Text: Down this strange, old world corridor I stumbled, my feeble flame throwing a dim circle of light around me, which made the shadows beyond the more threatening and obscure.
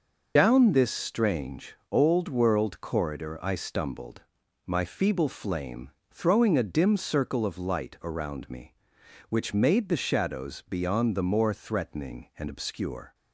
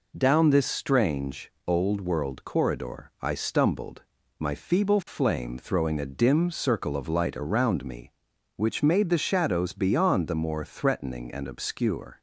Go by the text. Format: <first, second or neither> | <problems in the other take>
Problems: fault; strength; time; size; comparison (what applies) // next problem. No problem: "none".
second | loses the start of "Down"; at 0.3 s; 70 ms // pauses between "flame" and "throwing"; slight; at 5.9 s; 0.20 s long